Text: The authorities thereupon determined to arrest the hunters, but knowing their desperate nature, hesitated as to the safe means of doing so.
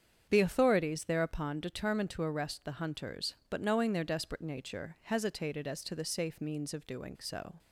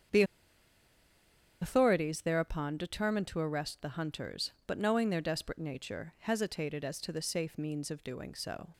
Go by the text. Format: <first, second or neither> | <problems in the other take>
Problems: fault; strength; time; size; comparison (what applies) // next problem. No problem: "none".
first | starts louder than the rest; strong; until 2.5 s; 8 dB; strong in the first // pauses between "The" and "authorities"; strong; at 0.2 s; 1.3 s long